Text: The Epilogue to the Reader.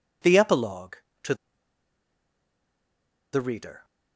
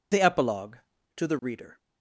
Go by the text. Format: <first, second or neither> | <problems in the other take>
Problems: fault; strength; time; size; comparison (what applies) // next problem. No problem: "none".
second | pauses between "to" and "the"; strong; at 1.3 s; 1.9 s long